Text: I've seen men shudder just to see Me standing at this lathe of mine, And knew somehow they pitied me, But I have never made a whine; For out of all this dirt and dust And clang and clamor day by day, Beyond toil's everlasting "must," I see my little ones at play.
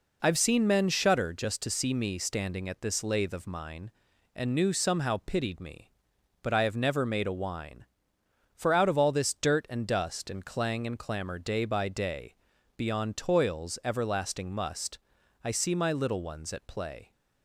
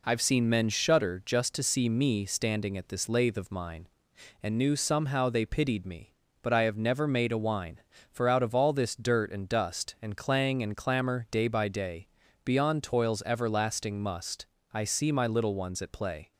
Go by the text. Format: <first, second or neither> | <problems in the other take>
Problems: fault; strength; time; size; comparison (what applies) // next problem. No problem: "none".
second | skips "they"; at 5.2 s